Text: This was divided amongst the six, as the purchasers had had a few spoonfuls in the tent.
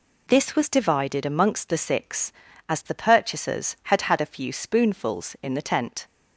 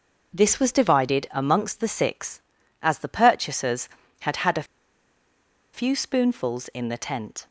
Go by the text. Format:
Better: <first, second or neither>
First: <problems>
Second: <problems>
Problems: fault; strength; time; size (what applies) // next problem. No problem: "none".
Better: first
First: none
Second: pauses between "a" and "few"; at 4.6 s; 1.0 s long